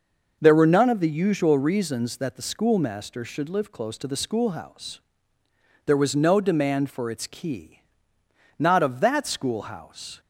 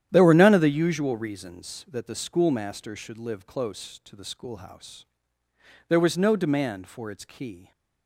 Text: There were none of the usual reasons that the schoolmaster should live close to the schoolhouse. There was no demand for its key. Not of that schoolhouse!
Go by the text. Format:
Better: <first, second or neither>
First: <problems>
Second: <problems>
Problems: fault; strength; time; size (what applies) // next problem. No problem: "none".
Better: first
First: none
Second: starts louder than the rest; strong; until 1.1 s; 10.5 dB // stops before "Not of that schoolhouse"; at 7.7 s